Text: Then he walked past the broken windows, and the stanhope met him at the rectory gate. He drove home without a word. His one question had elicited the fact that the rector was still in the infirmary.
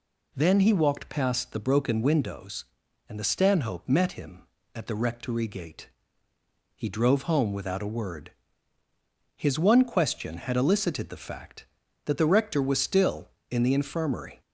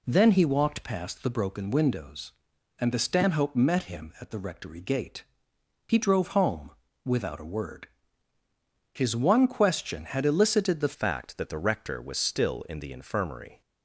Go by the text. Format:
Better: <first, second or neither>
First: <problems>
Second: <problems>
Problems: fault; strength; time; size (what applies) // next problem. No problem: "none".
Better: first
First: none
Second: pauses between "home" and "without"; slight; at 6.7 s; 0.34 s long // changes voice at "fact"; from 10.9 s on; 2.7 s long